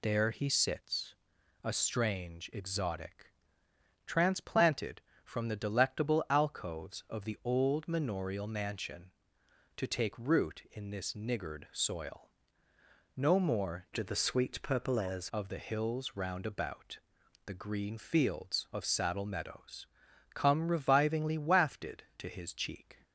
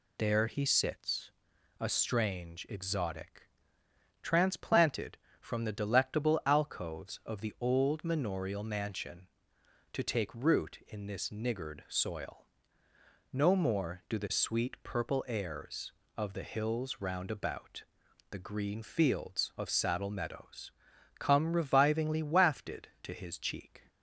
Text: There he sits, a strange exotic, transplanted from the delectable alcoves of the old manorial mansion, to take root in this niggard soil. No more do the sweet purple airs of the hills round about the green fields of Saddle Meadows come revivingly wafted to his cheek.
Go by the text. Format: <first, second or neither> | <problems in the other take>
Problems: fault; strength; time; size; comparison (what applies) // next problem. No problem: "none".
second | changes voice from "do" to "airs"; from 13.9 to 15.2 s; 1.3 s long // pauses between "about" and "the"; noticeable; at 16.9 s; 0.48 s long; noticeable in the second // pauses between "Meadows" and "come"; noticeable; at 19.8 s; 0.48 s long; noticeable in the second